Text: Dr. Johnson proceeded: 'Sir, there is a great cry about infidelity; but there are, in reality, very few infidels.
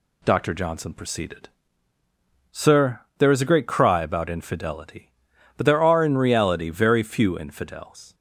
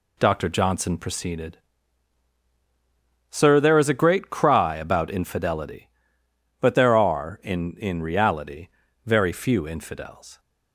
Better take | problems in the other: first | says "in" twice; at 7.7 s

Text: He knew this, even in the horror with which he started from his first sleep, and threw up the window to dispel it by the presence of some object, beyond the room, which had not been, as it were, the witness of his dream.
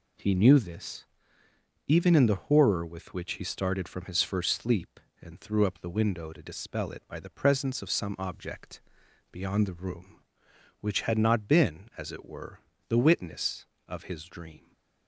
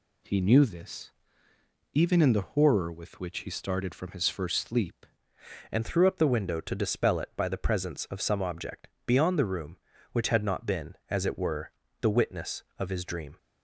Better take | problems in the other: first | changes voice at "and"; from 5.7 s on; 7.6 s long

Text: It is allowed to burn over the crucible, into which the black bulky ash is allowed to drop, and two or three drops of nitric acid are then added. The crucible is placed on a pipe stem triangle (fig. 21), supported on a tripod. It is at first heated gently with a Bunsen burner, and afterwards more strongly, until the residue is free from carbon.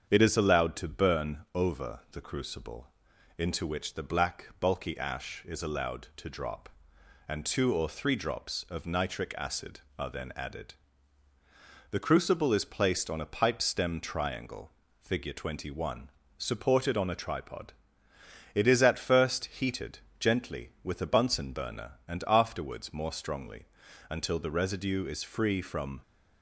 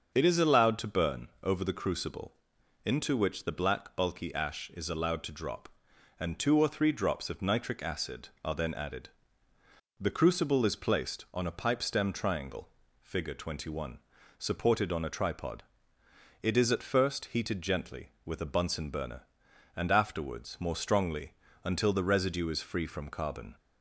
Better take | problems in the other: second | starts louder than the rest; strong; until 1.1 s; 7.5 dB; also in the second // pauses between "heated" and "gently"; slight; at 19.9 s; 0.22 s long // stops before "carbon"; at 26.0 s

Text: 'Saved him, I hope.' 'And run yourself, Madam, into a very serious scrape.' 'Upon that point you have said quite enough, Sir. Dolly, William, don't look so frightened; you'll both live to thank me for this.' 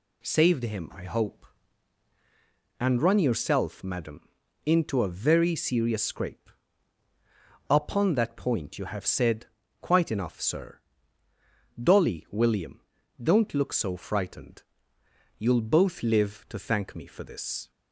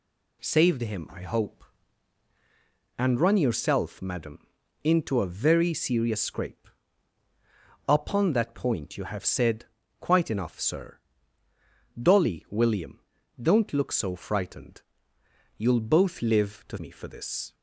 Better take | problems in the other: first | pauses between "said" and "quite"; slight; at 9.6 s; 0.34 s long; slight in the first // skips "thank"; at 16.7 s

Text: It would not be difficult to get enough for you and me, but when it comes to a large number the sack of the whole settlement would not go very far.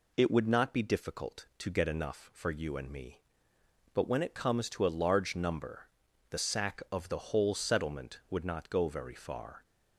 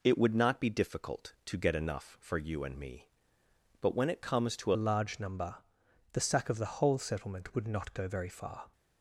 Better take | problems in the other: first | changes voice at "a"; from 4.7 s on; 4.0 s long // pauses between "number" and "the"; noticeable; at 5.5 s; 0.56 s long; also in the first

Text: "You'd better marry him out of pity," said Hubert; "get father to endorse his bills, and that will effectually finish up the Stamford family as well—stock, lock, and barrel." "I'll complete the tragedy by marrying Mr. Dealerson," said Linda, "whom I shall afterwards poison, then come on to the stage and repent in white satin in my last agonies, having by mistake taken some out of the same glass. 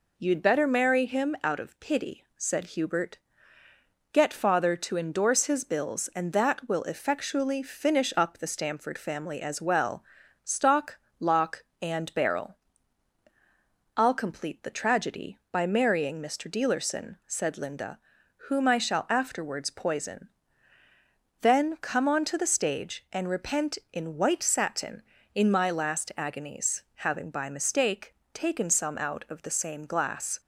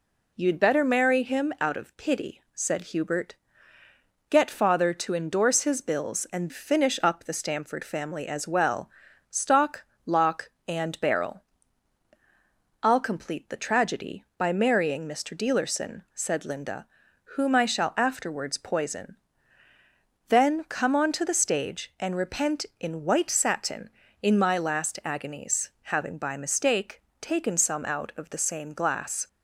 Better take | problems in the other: first | skips "that will effectually"; at 6.4 s // pauses between "mistake" and "taken"; slight; at 27.0 s; 0.18 s long; slight in the first

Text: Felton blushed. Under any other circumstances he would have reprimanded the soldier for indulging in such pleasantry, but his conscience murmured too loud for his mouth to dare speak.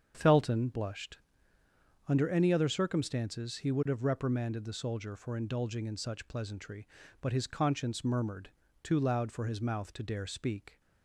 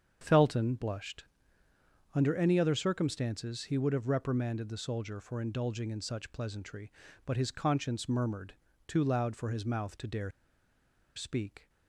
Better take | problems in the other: first | starts louder than the rest; strong; until 1.2 s; 7 dB; strong in the first // pauses between "murmured" and "too"; slight; at 8.5 s; 0.32 s long; slight in the first // pauses between "dare" and "speak"; noticeable; at 10.3 s; 0.85 s long

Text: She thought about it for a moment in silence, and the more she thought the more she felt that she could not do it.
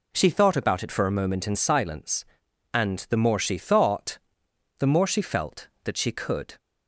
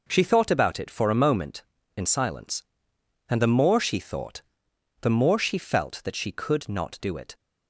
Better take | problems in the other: second | pauses between "thought" and "the"; noticeable; at 4.1 s; 0.62 s long; noticeable in the second // stops before "not do it"; at 6.5 s

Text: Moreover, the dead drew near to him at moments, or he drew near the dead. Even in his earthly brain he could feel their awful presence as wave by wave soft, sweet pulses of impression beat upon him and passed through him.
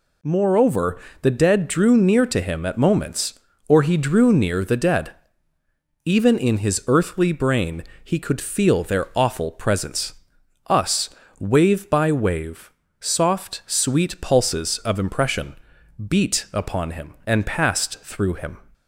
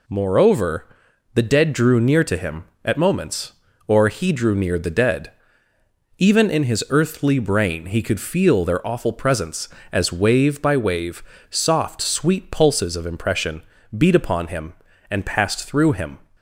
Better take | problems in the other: second | pauses between "brain" and "he"; slight; at 7.8 s; 0.20 s long // says "us" for "as"; at 10.6 s // pauses between "wave" and "soft"; slight; at 12.7 s; 0.28 s long; slight in the second // pauses between "impression" and "beat"; noticeable; at 15.5 s; 0.52 s long; slight in the second

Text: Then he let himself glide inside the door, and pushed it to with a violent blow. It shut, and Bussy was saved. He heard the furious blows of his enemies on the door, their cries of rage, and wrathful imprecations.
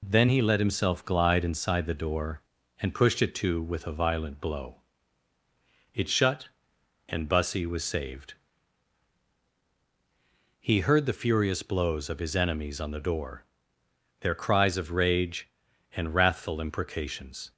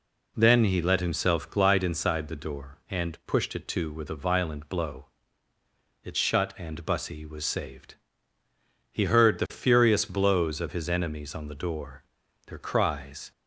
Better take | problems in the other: first | stops before "of rage and wrathful imprecations"; at 13.3 s

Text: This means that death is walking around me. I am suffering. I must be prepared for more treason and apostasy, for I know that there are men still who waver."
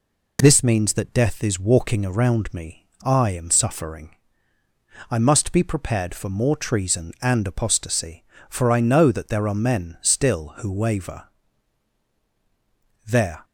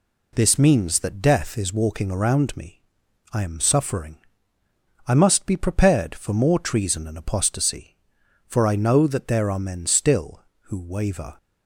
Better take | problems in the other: second | goes on to say "There"; slight; from 13.0 s on; 0.38 s long

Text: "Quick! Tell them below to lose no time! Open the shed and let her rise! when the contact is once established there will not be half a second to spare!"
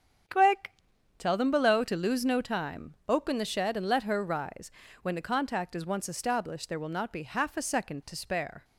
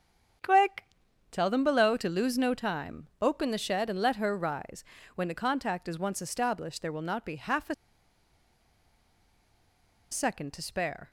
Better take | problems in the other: first | starts louder than the rest; strong; until 1.8 s; 8 dB; strong in the first // pauses between "a" and "second"; strong; at 7.7 s; 2.3 s long

